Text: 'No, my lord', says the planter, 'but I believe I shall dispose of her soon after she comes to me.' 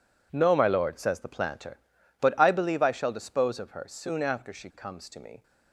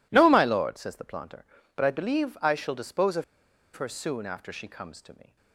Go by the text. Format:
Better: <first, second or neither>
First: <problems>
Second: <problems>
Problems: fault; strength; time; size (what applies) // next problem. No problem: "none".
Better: first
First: none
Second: pauses between "of" and "her"; noticeable; at 3.2 s; 0.51 s long